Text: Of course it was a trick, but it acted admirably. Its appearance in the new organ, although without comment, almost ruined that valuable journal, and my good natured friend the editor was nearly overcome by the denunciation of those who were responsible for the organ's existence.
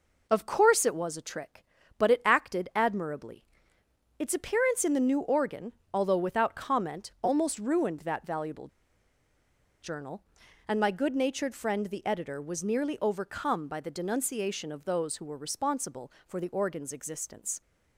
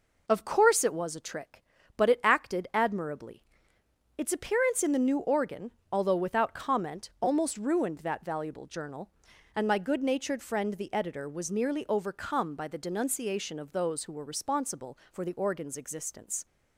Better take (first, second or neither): second